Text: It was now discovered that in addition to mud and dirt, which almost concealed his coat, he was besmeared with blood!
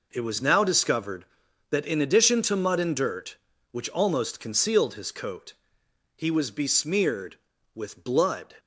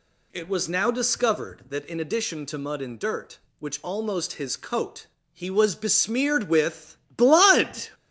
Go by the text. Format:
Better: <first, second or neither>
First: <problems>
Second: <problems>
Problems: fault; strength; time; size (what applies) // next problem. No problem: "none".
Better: first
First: none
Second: skips "concealed"; at 4.3 s // pauses between "with" and "blood"; slight; at 6.9 s; 0.20 s long